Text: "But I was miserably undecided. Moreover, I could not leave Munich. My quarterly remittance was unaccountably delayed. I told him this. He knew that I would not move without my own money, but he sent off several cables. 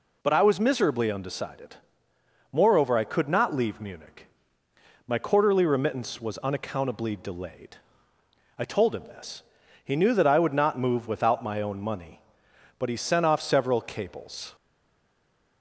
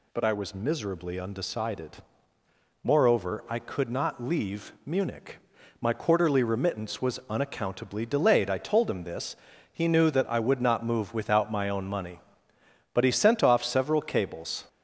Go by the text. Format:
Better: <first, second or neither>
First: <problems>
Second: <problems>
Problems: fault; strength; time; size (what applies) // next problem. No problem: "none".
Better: second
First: stays silent after the last word; from 14.5 s on; 1.1 s long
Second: none